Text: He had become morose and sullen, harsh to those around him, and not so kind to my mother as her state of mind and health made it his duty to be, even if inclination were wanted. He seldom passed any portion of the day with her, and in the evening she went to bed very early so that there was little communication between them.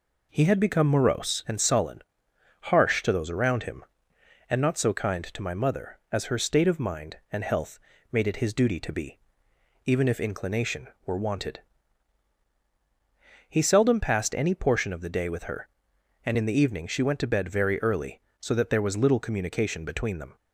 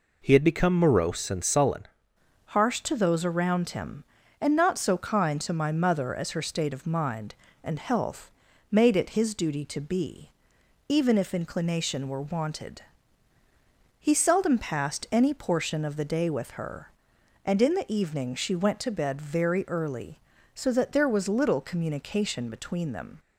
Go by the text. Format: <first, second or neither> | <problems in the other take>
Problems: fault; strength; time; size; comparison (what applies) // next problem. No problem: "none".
first | changes voice at "harsh"; from 2.4 s on; 20.7 s long // pauses between "health" and "made"; at 8.2 s; 0.40 s long; slight in the first